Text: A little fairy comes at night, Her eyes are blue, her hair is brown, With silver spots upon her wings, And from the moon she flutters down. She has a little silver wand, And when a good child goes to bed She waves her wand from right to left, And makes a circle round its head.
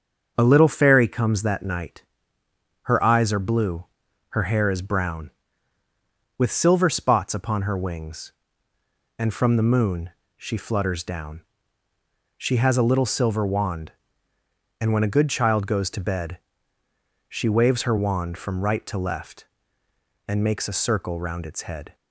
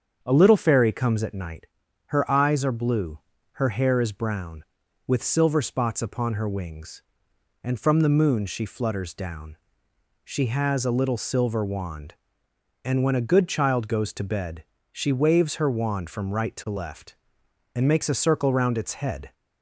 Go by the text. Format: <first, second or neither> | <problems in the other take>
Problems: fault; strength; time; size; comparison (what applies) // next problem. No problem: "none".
second | starts louder than the rest; until 1.3 s; 7 dB; strong in the second // says "that" for "at"; at 1.4 s // pauses between "moon" and "she"; slight; at 10.0 s; 0.26 s long // pauses between "bed" and "She"; noticeable; at 16.3 s; 0.92 s long; slight in the second